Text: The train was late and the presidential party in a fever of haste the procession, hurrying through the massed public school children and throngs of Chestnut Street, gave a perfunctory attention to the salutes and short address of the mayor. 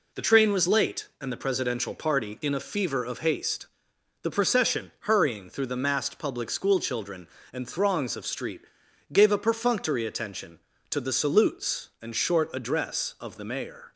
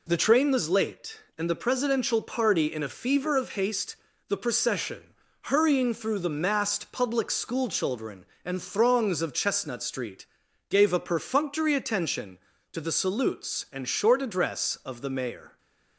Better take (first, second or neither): second